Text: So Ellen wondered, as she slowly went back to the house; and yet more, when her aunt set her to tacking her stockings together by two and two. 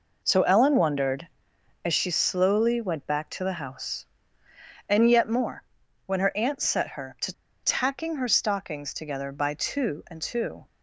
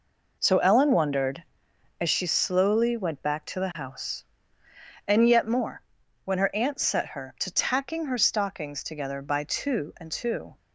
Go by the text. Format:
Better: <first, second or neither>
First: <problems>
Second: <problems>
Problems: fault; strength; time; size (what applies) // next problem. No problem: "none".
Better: second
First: pauses between "to" and "tacking"; slight; at 7.3 s; 0.30 s long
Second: none